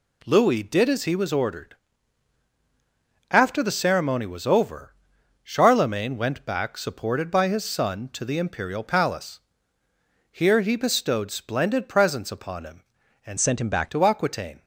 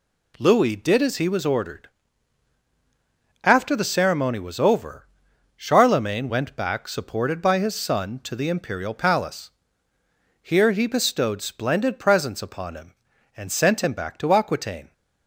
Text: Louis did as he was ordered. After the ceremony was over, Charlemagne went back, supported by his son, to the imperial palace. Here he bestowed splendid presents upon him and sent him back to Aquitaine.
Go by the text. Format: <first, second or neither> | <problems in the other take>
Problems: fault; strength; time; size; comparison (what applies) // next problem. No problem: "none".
second | changes voice from "sent" to "back"; from 13.3 to 13.9 s; 0.6 s long